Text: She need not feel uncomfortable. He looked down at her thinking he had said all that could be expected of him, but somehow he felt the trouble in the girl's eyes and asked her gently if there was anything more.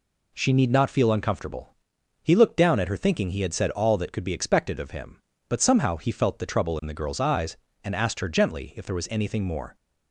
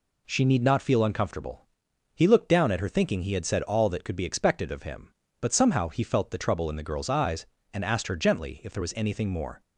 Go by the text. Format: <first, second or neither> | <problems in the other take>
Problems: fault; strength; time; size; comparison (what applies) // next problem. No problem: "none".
neither | none